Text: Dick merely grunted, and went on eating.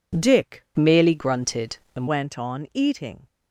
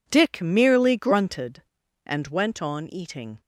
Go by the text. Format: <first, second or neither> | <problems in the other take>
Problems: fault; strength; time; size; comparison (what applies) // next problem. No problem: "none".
second | changes voice from "merely" to "and"; from 0.7 to 2.0 s; 1.3 s long